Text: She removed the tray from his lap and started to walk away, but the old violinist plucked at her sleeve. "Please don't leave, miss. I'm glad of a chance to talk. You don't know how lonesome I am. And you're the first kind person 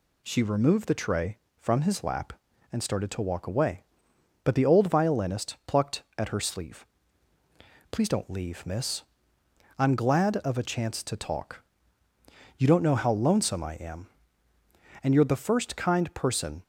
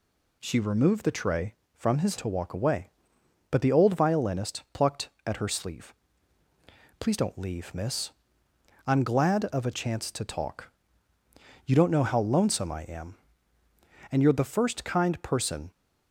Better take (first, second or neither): first